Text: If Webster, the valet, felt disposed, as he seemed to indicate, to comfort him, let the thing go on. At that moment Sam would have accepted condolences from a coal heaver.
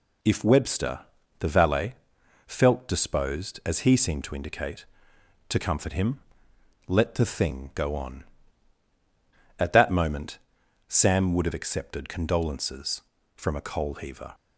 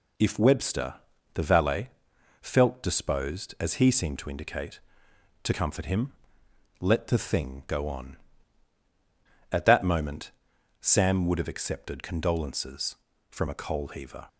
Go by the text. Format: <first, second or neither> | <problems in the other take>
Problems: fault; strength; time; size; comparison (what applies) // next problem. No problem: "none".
neither | pauses between "moment" and "Sam"; noticeable; the same in both